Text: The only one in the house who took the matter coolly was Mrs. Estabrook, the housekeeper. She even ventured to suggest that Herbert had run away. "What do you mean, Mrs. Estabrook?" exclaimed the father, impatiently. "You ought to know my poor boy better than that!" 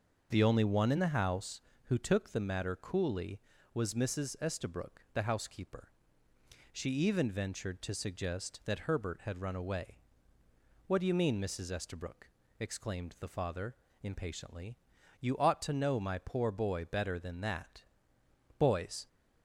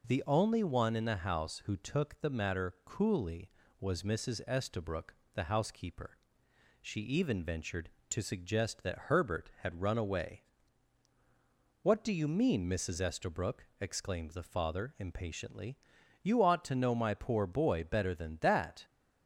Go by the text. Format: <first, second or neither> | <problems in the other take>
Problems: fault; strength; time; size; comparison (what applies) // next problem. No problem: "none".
second | starts louder than the rest; until 1.3 s; 6.5 dB // goes on to say "Boys"; slight; from 18.5 s on; 0.48 s long